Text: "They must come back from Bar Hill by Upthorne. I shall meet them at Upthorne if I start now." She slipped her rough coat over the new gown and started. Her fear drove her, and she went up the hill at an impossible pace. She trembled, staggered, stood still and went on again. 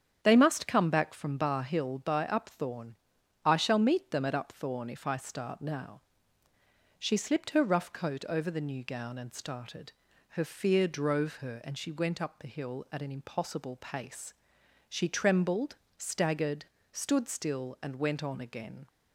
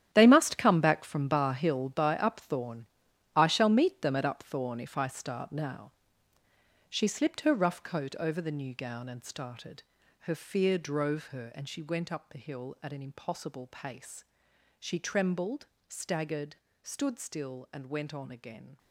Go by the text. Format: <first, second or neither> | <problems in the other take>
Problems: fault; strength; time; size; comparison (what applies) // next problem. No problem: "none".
first | gets quieter; strong; throughout; 12.5 dB // starts louder than the rest; strong; until 1.1 s; 10.5 dB; strong in the first